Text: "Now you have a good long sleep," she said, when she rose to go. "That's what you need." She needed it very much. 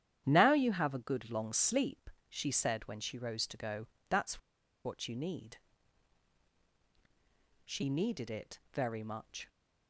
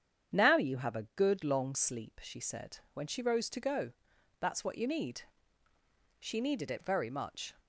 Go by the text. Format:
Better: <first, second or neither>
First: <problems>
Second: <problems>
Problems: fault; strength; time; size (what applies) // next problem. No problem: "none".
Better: second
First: starts louder than the rest; strong; until 1.2 s; 10 dB // pauses between "That's" and "what"; at 4.3 s; 0.45 s long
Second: starts louder than the rest; strong; until 1.4 s; 8 dB